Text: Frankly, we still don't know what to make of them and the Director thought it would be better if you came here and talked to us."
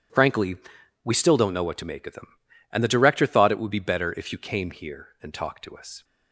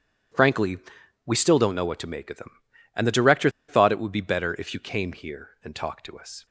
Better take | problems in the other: first | pauses between "Director" and "thought"; slight; at 3.4 s; 0.19 s long

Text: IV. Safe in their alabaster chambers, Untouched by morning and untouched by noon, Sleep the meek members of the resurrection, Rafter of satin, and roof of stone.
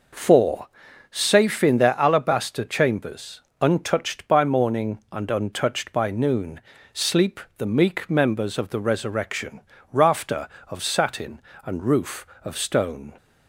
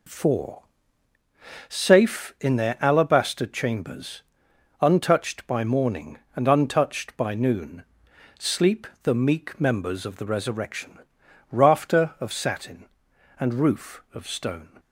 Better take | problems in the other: neither | pauses between "Sleep" and "the"; slight; the same in both

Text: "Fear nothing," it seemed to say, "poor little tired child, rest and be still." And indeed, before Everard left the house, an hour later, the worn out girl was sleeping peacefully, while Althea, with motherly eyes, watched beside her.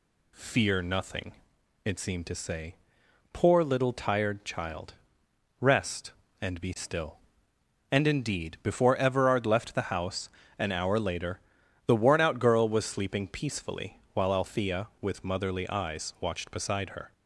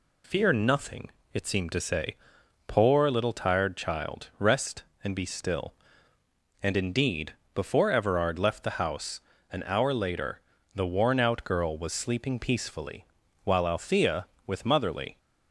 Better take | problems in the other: first | stops before "eyes watched beside her"; at 15.1 s

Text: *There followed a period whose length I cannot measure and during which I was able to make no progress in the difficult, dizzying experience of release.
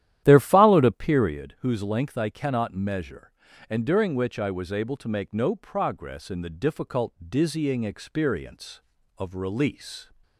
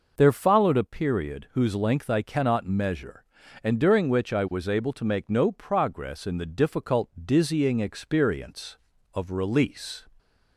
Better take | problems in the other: second | starts louder than the rest; strong; until 1.4 s; 12 dB

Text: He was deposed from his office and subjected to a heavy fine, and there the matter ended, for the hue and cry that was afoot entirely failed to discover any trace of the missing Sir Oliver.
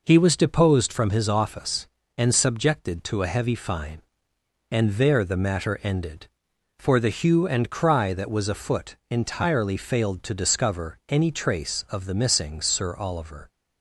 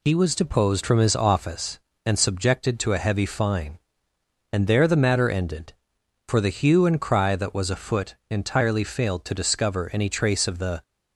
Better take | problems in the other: first | stops before "missing Sir Oliver"; at 10.8 s

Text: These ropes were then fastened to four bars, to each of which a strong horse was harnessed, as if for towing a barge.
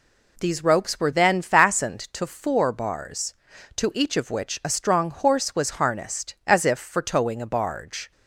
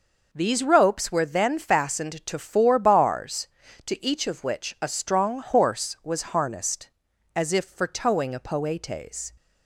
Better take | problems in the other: first | says "poetes" for "barge"; at 8.3 s

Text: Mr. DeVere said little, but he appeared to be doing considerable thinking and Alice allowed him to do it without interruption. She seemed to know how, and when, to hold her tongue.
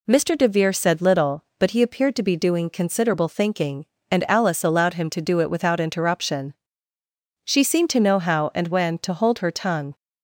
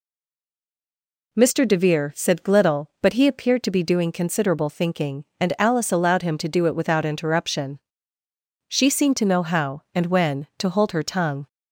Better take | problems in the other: first | stays silent before the first word; noticeable; until 1.3 s; 1.3 s long

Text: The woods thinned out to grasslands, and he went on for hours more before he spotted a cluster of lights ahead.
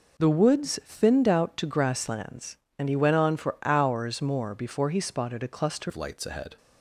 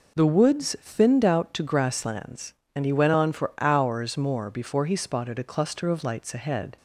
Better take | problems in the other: second | changes voice at "of"; from 5.8 s on; 0.7 s long

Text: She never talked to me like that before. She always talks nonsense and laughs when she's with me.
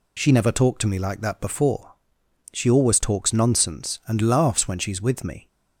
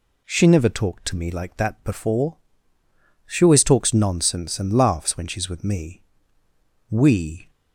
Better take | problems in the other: first | goes on to say "We"; from 6.8 s on; 0.60 s long

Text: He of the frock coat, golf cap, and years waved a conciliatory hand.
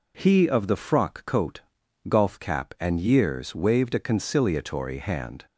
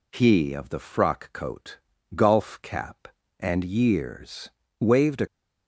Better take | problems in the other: first | pauses between "years" and "waved"; slight; at 4.4 s; 0.30 s long // stops before "conciliatory hand"; at 5.2 s

